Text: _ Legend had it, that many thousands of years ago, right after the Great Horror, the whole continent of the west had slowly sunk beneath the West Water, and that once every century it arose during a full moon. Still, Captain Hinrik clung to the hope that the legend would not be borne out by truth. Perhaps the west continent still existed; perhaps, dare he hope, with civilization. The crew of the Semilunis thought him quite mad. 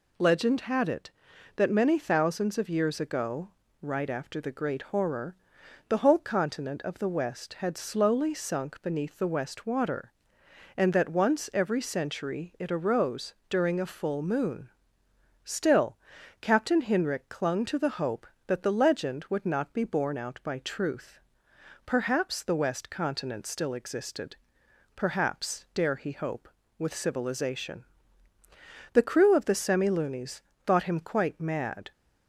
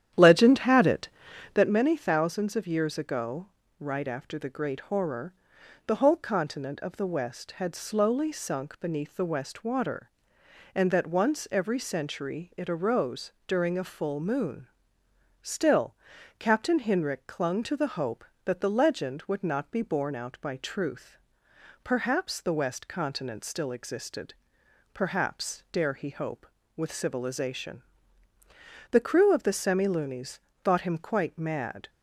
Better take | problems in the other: first | starts louder than the rest; strong; until 1.8 s; 10.5 dB // pauses between "arose" and "during"; slight; at 13.3 s; 0.16 s long; slight in the first // pauses between "Semilunis" and "thought"; slight; at 30.3 s; 0.24 s long; slight in the first

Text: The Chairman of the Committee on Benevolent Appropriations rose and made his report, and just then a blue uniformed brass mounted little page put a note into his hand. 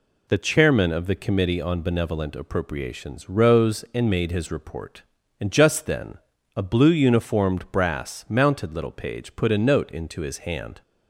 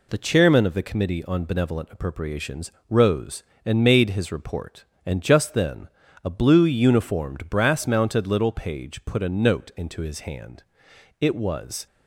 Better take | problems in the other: first | pauses between "Appropriations" and "rose"; slight; at 2.7 s; 0.18 s long // pauses between "then" and "a"; slight; at 5.8 s; 0.36 s long; slight in the first // goes on to say "It was"; noticeable; from 11.1 s on; 0.66 s long

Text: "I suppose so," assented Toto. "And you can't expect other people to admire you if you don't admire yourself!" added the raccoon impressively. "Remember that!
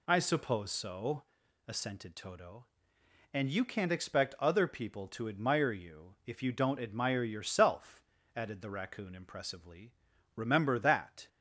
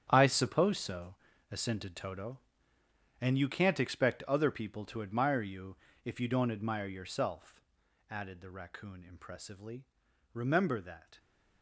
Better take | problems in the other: first | gets quieter; strong; throughout; 13 dB // pauses between "you" and "if"; slight; at 5.7 s; 0.30 s long

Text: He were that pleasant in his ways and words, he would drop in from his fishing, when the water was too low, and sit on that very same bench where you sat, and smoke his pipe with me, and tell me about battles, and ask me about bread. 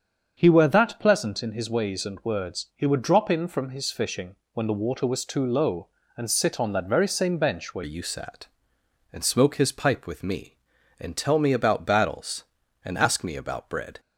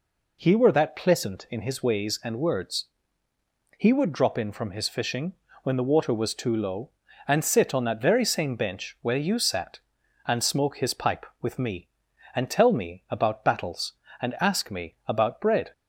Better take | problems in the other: second | starts louder than the rest; strong; until 1.3 s; 7 dB // changes voice at "you"; from 7.8 s on; 6.1 s long

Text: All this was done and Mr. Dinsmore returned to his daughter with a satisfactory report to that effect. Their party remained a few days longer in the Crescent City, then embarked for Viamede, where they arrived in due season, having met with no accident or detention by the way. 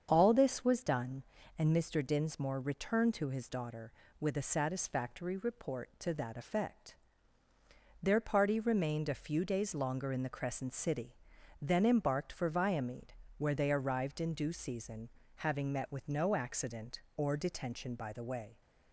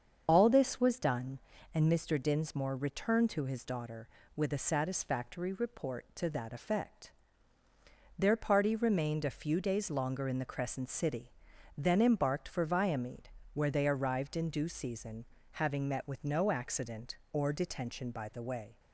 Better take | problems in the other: first | loses the start of "All"; at 0.2 s; 45 ms // starts louder than the rest; until 1.2 s; 7 dB; strong in the first

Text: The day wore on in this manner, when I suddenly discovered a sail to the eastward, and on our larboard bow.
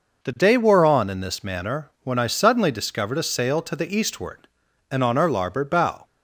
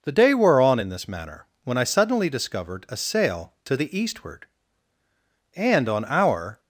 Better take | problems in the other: first | stops before "larboard bow"; at 6.5 s

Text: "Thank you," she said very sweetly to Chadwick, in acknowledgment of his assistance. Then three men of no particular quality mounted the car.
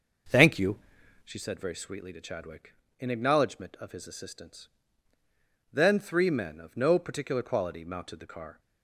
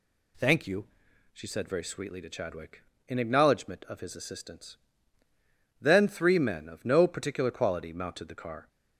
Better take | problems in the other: second | starts louder than the rest; until 1.4 s; 6 dB

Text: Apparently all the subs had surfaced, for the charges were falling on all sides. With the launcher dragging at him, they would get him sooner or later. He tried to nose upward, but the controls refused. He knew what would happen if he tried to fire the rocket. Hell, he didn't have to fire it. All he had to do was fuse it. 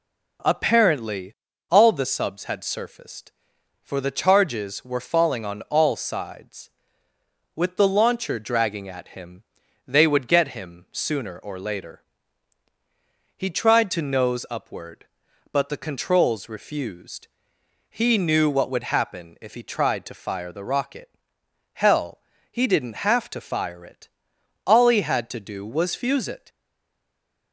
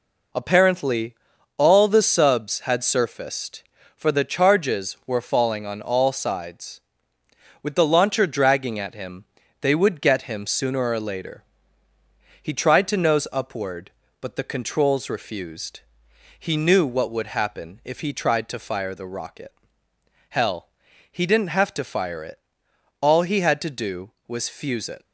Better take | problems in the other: second | pauses between "Apparently" and "all"; slight; at 1.3 s; 0.34 s long; also in the second // stays silent after the last word; from 26.4 s on; 1.1 s long

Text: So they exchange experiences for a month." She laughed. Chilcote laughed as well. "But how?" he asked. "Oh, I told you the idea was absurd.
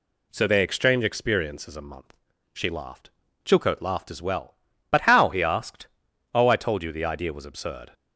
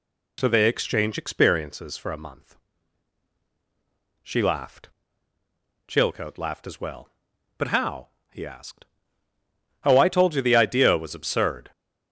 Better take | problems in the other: second | skips "for"; at 1.7 s

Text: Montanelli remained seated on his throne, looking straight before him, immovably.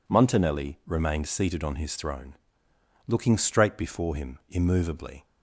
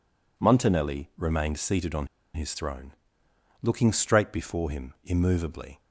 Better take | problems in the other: first | pauses between "on" and "his"; slight; at 2.0 s; 0.27 s long

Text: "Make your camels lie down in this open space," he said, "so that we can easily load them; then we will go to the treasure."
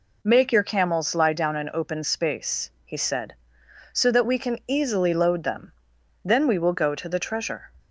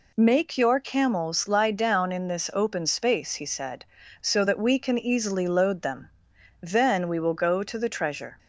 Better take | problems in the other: second | skips "this"; at 1.7 s

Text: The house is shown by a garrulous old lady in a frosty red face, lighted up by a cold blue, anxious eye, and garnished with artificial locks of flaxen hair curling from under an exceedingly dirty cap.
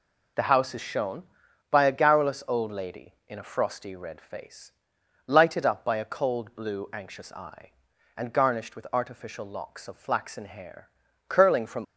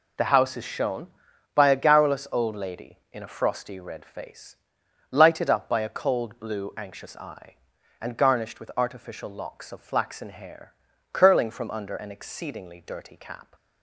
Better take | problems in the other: second | pauses between "hair" and "curling"; at 10.9 s; 0.38 s long; also in the second // stops before "under an exceedingly dirty cap"; at 11.8 s

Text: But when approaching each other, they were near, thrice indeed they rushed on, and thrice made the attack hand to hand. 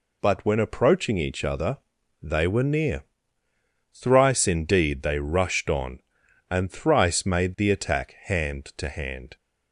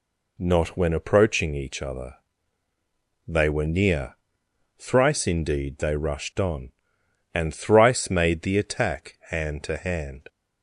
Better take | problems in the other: first | says "Not" for "But"; at 0.3 s

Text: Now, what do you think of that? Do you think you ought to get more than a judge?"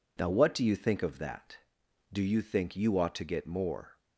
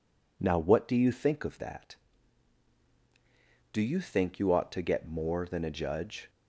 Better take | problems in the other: second | stops before "than a judge"; at 3.9 s

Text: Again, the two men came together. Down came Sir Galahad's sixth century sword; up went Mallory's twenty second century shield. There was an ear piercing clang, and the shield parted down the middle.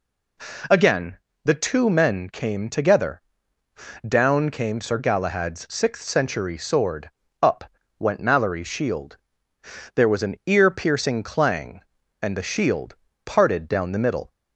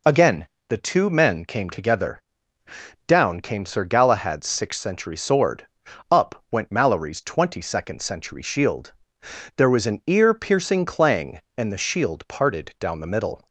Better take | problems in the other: second | pauses between "up" and "went"; slight; at 7.6 s; 0.34 s long // skips "twenty second century"; at 8.6 s // pauses between "shield" and "parted"; slight; at 12.9 s; 0.32 s long

